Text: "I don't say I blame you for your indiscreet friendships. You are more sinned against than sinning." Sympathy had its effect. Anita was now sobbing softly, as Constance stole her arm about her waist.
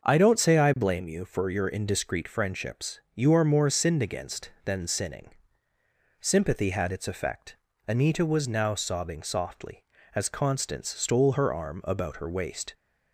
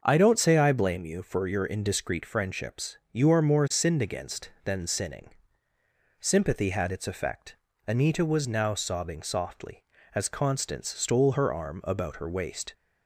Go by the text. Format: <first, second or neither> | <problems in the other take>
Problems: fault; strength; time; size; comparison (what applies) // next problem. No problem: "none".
neither | starts louder than the rest; the same in both